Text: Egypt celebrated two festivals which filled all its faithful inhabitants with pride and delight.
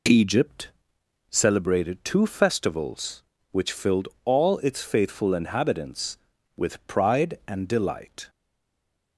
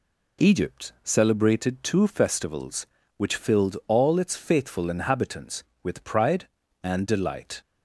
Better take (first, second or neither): second